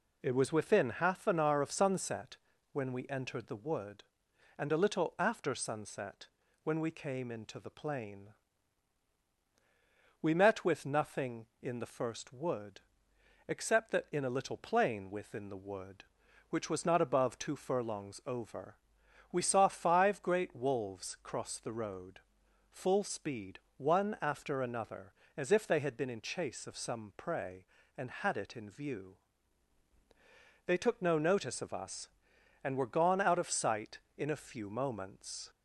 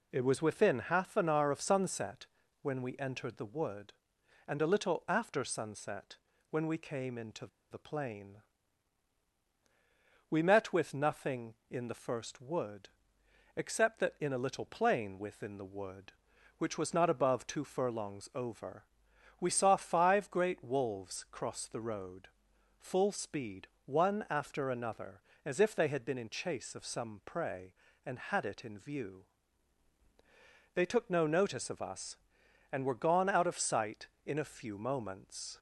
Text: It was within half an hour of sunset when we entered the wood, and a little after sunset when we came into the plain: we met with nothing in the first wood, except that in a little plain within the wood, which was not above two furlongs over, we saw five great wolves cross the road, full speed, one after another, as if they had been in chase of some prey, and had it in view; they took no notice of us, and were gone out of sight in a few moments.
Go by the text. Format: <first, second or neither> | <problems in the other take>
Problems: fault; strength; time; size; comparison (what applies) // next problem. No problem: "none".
first | pauses between "sunset" and "when"; slight; at 2.2 s; 0.36 s long; slight in the first // pauses between "sunset" and "when"; slight; at 6.1 s; 0.34 s long; also in the first // pauses between "into" and "the"; slight; at 7.4 s; 0.24 s long